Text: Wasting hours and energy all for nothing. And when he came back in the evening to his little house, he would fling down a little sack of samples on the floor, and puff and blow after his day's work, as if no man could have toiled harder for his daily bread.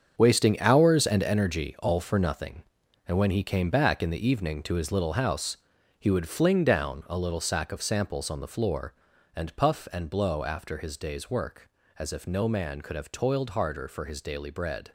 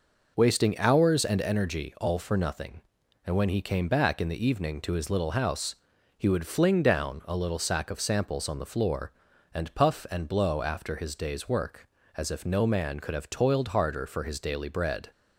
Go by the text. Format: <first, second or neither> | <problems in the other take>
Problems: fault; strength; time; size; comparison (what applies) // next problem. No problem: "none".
second | gets quieter; strong; throughout; 11 dB